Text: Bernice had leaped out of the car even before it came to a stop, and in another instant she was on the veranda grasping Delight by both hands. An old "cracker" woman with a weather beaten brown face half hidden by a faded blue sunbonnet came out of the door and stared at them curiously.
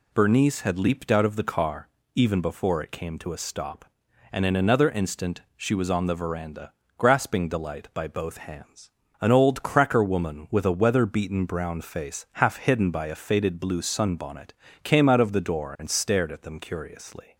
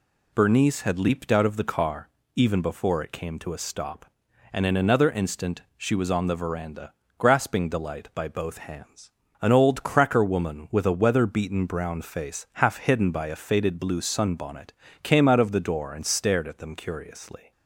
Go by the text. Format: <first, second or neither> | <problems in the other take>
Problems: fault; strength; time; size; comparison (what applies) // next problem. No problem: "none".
neither | pauses between "car" and "even"; slight; the same in both // pauses between "veranda" and "grasping"; slight; the same in both // pauses between "sunbonnet" and "came"; slight; the same in both